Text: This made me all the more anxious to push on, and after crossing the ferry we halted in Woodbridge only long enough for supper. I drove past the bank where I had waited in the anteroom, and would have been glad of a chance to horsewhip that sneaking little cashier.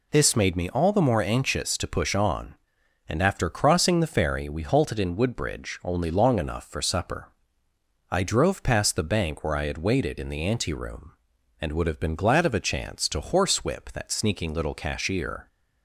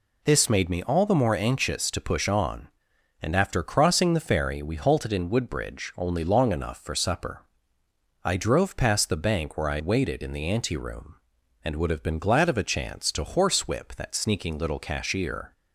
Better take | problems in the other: first | skips "had"; at 9.8 s

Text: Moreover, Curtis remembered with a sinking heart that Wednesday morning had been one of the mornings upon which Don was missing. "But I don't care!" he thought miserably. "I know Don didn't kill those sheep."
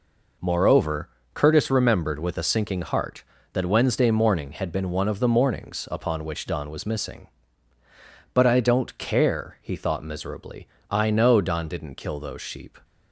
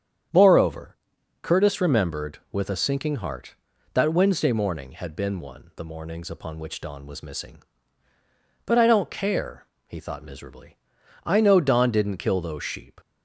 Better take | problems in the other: first | starts louder than the rest; strong; until 1.7 s; 8.5 dB // skips "of"; at 5.7 s

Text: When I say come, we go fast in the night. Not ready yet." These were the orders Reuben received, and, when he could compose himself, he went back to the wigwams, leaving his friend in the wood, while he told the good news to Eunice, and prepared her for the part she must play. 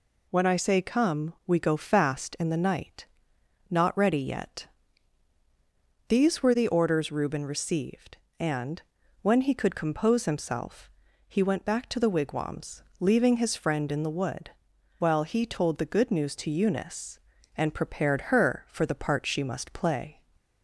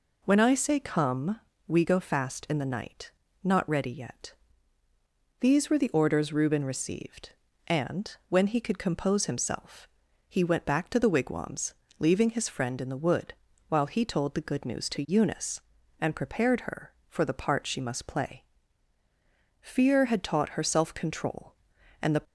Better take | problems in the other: first | goes on to say "Fear had taught her self control and the"; strong; from 19.6 s on; 2.6 s long

